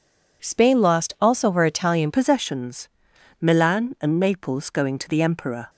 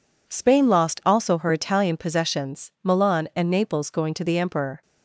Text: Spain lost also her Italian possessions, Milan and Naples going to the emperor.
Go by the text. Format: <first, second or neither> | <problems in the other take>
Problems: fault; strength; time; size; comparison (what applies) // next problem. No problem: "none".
second | changes voice at "possessions"; from 2.1 s on; 3.5 s long